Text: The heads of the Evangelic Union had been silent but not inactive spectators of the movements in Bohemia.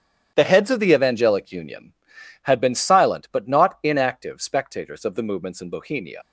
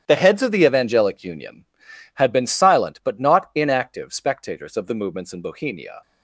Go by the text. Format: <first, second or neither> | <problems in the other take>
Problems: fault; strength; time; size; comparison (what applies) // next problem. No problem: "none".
second | starts louder than the rest; strong; until 1.3 s; 10 dB; strong in the second // leaves "Bohemia" unfinished; at 6.2 s; 75 ms